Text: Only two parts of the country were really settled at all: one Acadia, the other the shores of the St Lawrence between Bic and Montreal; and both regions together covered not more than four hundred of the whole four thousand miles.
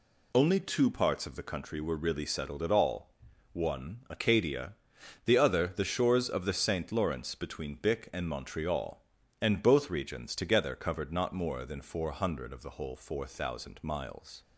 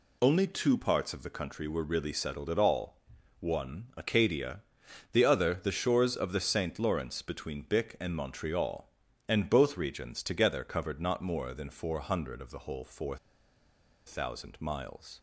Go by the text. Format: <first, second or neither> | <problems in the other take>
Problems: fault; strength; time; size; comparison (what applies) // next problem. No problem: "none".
first | pauses between "four" and "thousand"; noticeable; at 13.1 s; 0.88 s long